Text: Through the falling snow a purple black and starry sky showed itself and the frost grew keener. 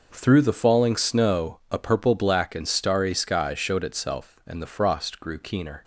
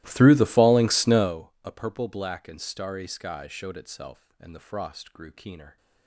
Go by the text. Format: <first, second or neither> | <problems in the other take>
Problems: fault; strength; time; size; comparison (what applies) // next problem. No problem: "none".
first | starts louder than the rest; strong; until 1.4 s; 17.5 dB